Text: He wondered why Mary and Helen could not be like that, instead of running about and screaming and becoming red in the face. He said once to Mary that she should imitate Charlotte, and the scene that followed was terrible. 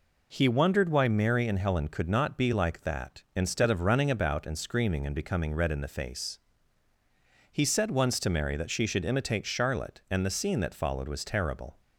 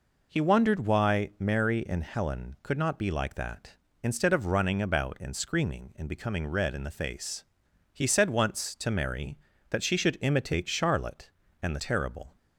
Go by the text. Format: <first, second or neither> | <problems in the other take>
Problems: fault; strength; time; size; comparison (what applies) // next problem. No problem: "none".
first | skips "scene that followed was"; at 11.7 s